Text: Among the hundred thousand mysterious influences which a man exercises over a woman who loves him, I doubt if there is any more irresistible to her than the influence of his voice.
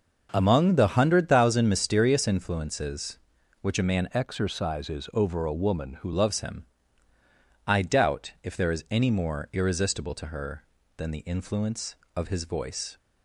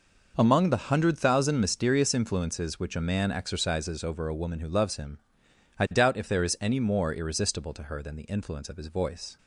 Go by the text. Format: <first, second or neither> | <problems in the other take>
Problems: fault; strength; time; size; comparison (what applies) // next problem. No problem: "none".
second | changes voice from "exercises" to "who"; from 4.1 to 6.1 s; 2.0 s long